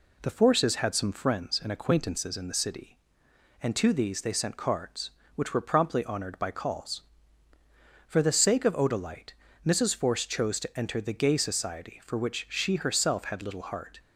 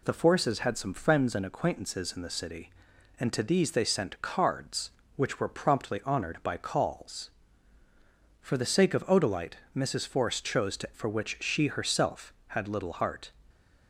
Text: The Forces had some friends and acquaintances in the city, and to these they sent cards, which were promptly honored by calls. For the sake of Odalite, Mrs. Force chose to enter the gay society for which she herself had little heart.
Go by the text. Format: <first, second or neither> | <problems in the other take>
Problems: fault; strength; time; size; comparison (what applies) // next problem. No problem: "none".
first | skips "enter the gay society"; at 10.9 s